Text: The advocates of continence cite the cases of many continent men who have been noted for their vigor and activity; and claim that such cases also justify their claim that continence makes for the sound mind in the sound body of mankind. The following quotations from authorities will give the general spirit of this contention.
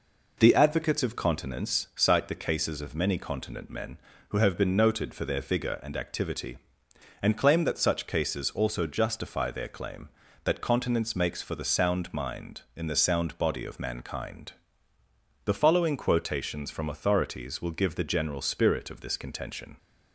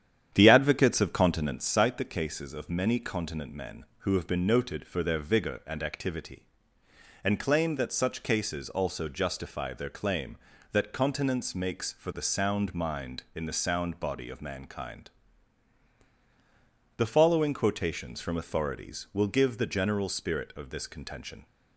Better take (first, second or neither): first